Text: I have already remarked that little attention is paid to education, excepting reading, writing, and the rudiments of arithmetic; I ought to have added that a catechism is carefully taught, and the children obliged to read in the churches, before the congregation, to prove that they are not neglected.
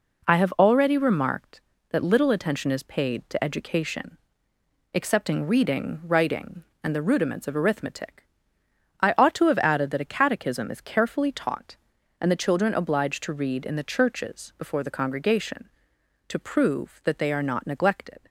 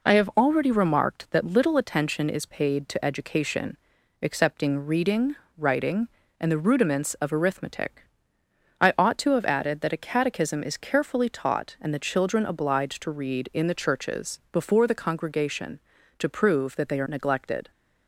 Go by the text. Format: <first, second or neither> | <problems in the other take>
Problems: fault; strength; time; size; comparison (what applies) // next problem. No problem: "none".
first | skips "not"; at 17.0 s